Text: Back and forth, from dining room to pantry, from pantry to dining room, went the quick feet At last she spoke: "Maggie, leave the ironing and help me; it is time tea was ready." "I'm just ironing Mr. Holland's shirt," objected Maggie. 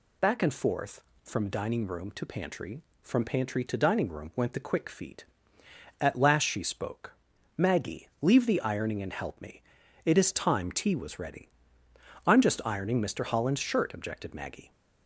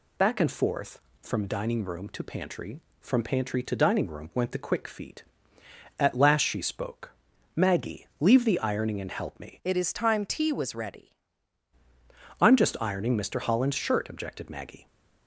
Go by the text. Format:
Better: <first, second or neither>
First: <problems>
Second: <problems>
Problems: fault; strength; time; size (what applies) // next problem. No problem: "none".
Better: first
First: none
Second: changes voice from "it" to "ready"; from 9.6 to 11.1 s; 1.5 s long